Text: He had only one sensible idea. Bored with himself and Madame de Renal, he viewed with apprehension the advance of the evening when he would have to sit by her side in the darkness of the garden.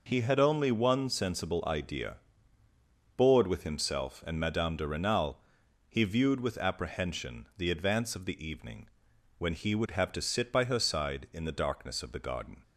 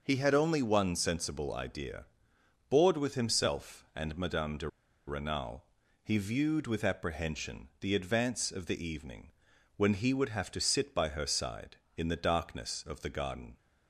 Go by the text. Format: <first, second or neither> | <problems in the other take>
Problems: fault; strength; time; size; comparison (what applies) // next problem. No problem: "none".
first | pauses between "de" and "Renal"; at 4.6 s; 0.39 s long // pauses between "evening" and "when"; noticeable; at 9.3 s; 0.46 s long; noticeable in the first